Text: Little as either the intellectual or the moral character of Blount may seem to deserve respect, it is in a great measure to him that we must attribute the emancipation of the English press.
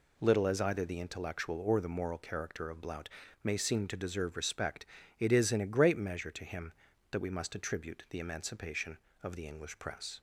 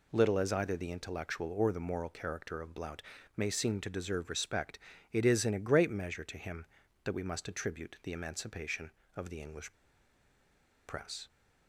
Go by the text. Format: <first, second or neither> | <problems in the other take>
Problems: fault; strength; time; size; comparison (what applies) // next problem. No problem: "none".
first | pauses between "Blount" and "may"; slight; at 3.0 s; 0.34 s long; slight in the first // pauses between "English" and "press"; at 9.7 s; 1.1 s long